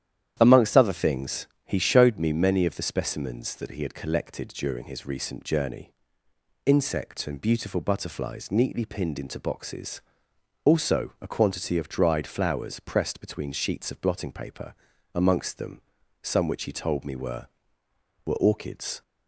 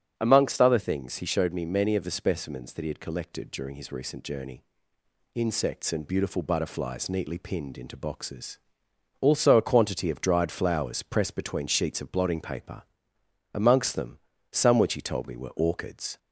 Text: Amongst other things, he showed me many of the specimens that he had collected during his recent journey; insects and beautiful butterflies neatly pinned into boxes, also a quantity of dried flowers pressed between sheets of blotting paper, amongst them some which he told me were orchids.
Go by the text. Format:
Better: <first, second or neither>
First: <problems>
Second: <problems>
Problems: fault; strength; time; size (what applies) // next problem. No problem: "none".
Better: second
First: starts louder than the rest; strong; until 1.4 s; 10.5 dB // pauses between "them" and "some"; at 15.8 s; 0.40 s long // says "were" twice; at 18.2 s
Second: starts louder than the rest; strong; until 1.1 s; 8.5 dB // pauses between "them" and "some"; slight; at 14.1 s; 0.34 s long